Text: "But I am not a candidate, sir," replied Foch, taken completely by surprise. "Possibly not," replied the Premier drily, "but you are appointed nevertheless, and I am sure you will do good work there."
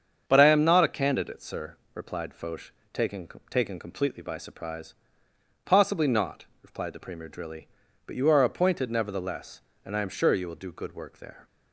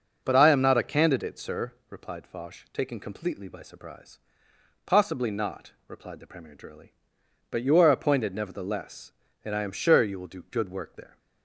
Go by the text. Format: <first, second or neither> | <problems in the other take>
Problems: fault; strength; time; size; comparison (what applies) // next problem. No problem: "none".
second | starts louder than the rest; strong; until 1.2 s; 7 dB // says "taken" twice; at 3.4 s